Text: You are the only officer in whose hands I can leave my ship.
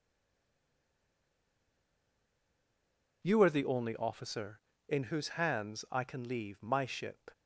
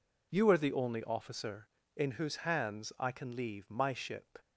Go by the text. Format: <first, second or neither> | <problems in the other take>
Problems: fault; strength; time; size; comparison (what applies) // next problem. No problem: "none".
second | stays silent before the first word; strong; until 3.2 s; 3.2 s long